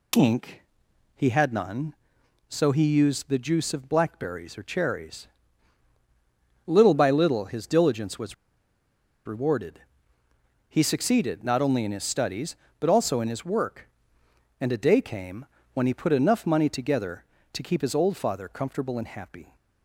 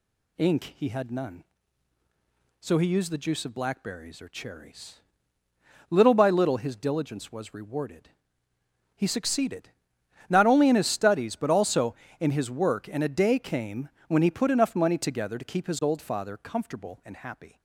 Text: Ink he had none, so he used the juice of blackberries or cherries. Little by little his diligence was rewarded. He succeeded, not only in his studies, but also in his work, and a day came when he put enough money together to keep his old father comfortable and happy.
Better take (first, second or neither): second